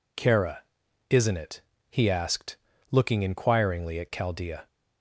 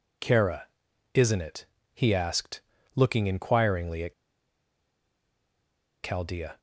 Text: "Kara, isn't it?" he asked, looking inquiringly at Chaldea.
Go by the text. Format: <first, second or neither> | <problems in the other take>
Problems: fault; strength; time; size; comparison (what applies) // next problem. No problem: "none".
first | pauses between "at" and "Chaldea"; strong; at 4.1 s; 1.8 s long